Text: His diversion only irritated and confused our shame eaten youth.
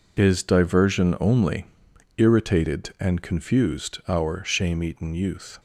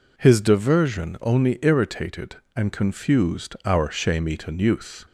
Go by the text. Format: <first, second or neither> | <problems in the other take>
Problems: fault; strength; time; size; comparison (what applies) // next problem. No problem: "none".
second | says "Is" for "His"; at 0.1 s // pauses between "only" and "irritated"; noticeable; at 1.6 s; 0.50 s long